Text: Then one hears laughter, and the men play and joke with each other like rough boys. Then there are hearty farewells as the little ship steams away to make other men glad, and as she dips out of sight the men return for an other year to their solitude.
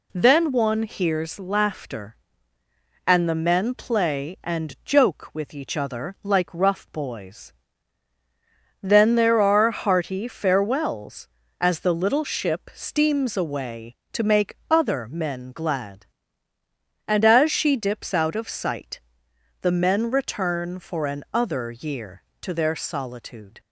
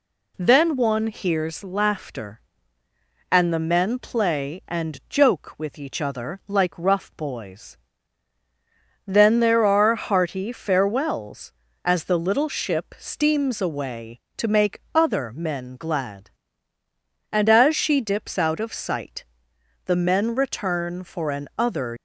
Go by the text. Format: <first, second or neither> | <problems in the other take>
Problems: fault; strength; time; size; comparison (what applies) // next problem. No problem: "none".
first | pauses between "sight" and "the"; noticeable; at 19.2 s; 0.62 s long; noticeable in the first // stops before "year to their solitude"; at 21.9 s